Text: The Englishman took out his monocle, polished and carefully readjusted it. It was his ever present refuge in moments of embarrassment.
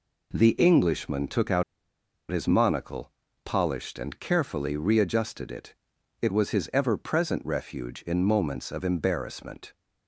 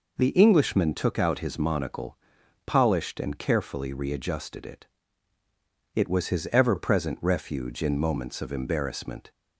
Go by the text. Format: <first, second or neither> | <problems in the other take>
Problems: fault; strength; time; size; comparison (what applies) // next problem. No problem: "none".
second | pauses between "out" and "his"; noticeable; at 1.6 s; 0.68 s long